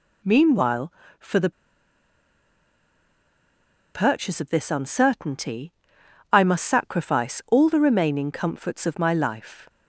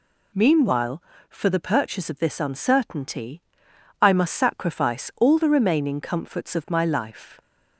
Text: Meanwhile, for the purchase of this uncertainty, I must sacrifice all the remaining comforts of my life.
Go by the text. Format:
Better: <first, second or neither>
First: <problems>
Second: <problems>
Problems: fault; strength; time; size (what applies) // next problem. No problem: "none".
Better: second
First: pauses between "the" and "purchase"; strong; at 1.5 s; 2.4 s long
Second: none